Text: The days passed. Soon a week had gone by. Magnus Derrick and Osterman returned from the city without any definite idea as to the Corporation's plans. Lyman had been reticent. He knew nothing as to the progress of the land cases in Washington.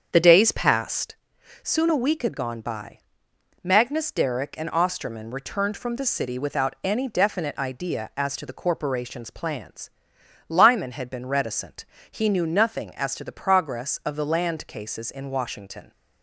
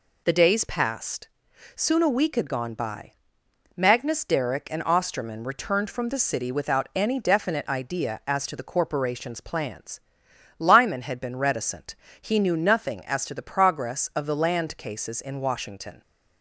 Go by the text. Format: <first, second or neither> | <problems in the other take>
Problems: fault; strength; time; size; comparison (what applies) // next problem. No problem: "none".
second | starts louder than the rest; strong; until 1.2 s; 7.5 dB